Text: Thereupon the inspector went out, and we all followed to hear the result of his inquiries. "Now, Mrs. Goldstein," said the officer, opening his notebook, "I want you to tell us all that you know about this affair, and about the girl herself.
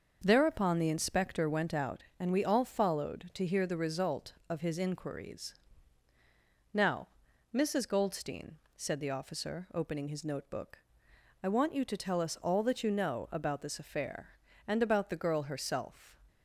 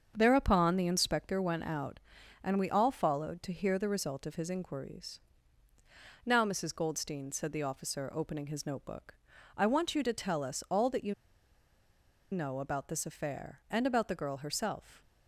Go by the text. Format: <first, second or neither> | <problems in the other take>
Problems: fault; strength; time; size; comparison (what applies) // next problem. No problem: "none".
first | starts louder than the rest; until 1.1 s; 7 dB; also in the first // pauses between "you" and "know"; at 11.1 s; 1.1 s long